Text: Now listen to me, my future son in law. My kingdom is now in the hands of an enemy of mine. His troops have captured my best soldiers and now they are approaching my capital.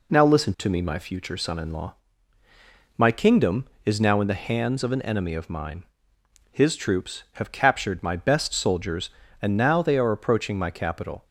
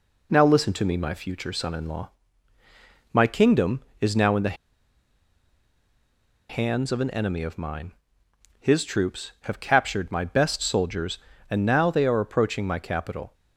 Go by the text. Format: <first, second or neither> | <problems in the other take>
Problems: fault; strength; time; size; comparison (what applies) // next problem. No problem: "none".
first | pauses between "the" and "hands"; strong; at 4.5 s; 1.9 s long